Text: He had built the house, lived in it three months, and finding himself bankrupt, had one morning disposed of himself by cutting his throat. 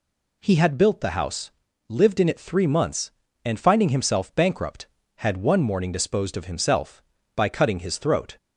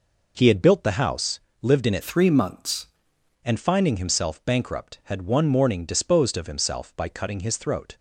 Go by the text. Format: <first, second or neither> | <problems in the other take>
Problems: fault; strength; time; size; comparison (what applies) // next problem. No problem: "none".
first | changes voice from "three" to "months"; from 2.0 to 2.8 s; 0.8 s long